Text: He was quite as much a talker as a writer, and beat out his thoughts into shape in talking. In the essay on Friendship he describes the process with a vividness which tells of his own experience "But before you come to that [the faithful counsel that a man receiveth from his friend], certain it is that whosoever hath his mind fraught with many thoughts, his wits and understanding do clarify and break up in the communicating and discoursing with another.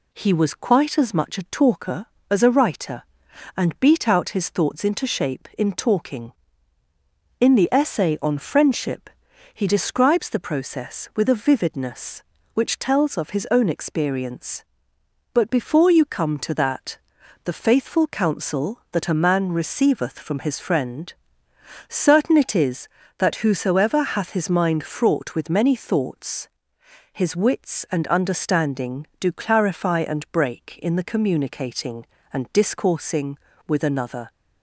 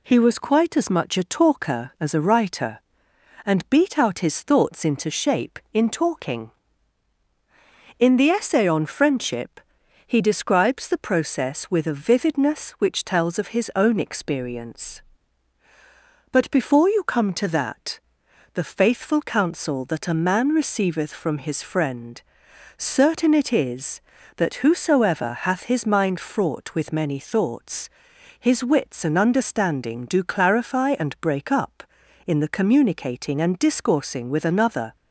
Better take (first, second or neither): second